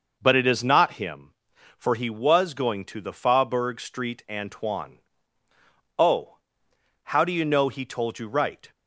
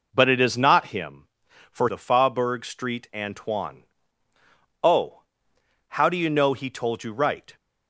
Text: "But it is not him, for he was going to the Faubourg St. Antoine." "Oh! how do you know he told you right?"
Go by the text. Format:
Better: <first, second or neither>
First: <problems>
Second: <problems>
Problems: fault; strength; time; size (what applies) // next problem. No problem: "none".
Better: first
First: none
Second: skips "he was going to"; at 1.8 s